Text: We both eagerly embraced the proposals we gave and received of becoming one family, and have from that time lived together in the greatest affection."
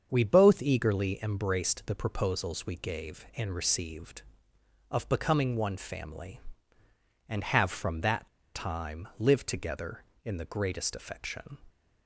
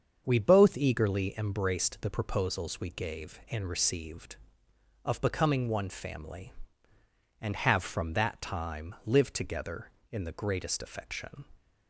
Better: second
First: starts louder than the rest; until 1.1 s; 7 dB // pauses between "that" and "time"; slight; at 8.2 s; 0.26 s long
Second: starts louder than the rest; until 1.2 s; 7 dB

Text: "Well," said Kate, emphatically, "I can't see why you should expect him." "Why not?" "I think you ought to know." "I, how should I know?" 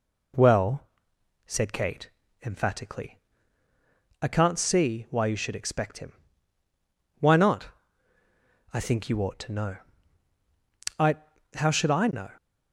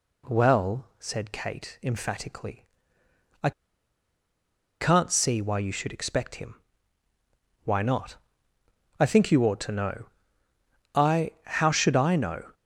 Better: first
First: none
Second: pauses between "I" and "can't"; strong; at 3.5 s; 1.2 s long

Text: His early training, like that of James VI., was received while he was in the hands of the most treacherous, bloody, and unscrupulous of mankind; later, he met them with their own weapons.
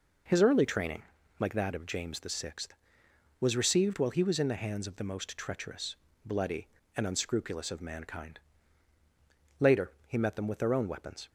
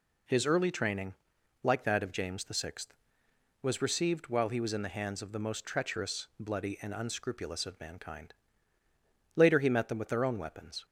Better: neither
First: none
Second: none

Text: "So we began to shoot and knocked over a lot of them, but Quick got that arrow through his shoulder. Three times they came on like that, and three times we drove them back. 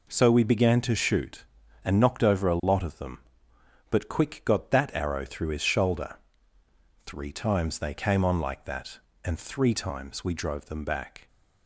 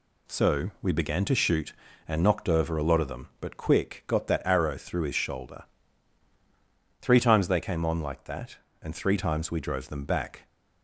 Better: neither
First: none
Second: none

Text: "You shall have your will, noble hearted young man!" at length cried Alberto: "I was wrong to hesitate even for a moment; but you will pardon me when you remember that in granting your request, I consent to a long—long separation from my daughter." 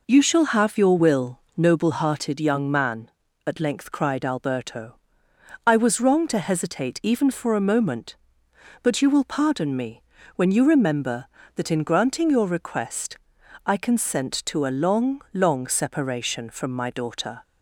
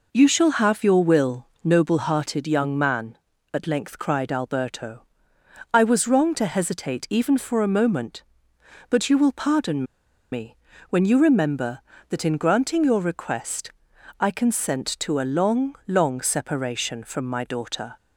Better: first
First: pauses between "me" and "when"; slight; at 10.0 s; 0.32 s long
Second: pauses between "pardon" and "me"; noticeable; at 9.8 s; 0.48 s long // pauses between "me" and "when"; slight; at 10.5 s; 0.32 s long

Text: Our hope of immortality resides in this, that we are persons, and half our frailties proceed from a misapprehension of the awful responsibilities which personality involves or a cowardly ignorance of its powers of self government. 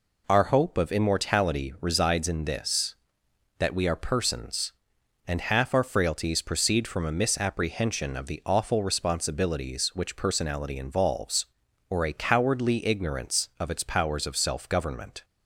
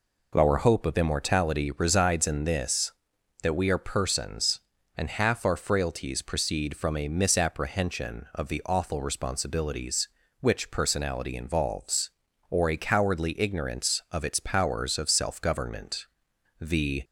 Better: first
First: none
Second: goes on to say "The"; slight; from 16.5 s on; 0.44 s long

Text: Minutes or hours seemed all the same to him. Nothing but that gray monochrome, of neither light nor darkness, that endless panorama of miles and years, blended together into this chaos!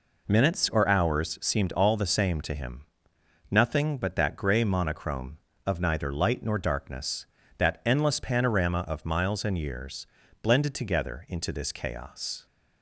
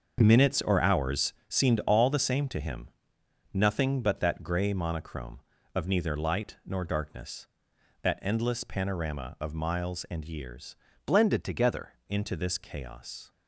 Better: first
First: none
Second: starts louder than the rest; until 1.2 s; 6.5 dB // pauses between "hours" and "seemed"; slight; at 1.3 s; 0.16 s long // changes voice from "blended" to "together"; from 11.0 to 11.9 s; 0.9 s long

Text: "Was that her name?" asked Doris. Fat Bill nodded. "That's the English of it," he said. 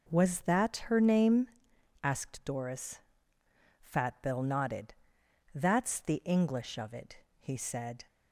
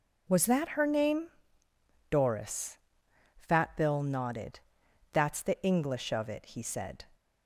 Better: first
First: none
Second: skips "asked"; at 1.6 s

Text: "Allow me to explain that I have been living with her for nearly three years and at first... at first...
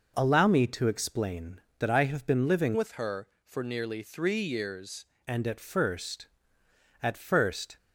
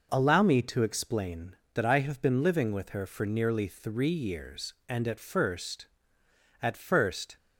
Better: second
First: changes voice from "with" to "years"; from 2.7 to 5.0 s; 2.3 s long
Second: none

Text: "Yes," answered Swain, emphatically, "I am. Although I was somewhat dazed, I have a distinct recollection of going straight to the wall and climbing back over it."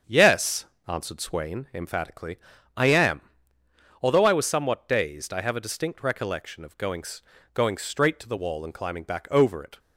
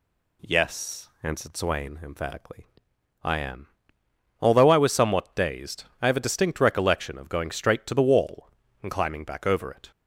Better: second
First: starts louder than the rest; strong; until 1.2 s; 7 dB // says "going" twice; at 7.5 s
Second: none

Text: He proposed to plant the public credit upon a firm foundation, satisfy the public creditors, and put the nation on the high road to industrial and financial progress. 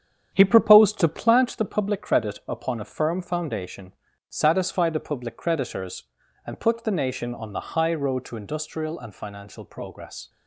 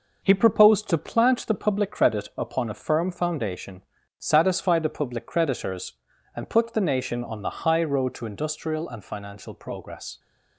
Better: second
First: starts louder than the rest; strong; until 1.4 s; 8.5 dB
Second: none

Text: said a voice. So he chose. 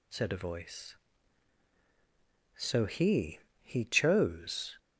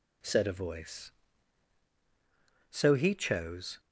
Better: second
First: says "he" twice; at 3.6 s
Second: none

